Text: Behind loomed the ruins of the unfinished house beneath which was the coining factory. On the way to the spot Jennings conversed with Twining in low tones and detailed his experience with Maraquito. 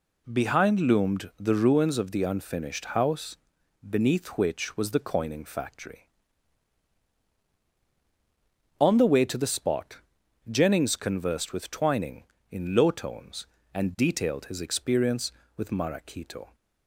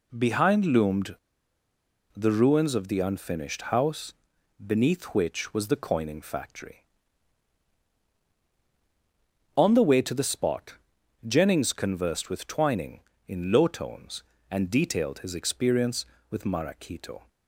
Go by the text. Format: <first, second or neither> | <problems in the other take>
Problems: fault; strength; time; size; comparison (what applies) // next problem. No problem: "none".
first | pauses between "loomed" and "the"; at 1.1 s; 0.99 s long // pauses between "house" and "beneath"; noticeable; at 4.1 s; 0.50 s long; noticeable in the first // pauses between "spot" and "Jennings"; noticeable; at 10.7 s; 0.52 s long; noticeable in the first